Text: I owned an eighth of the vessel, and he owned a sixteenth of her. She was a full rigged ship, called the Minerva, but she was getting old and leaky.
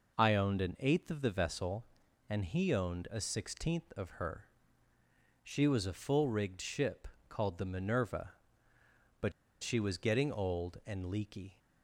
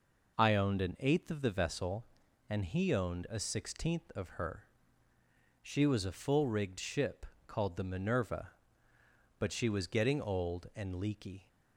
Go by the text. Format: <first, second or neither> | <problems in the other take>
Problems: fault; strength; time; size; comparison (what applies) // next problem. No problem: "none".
second | pauses between "but" and "she"; slight; at 9.3 s; 0.30 s long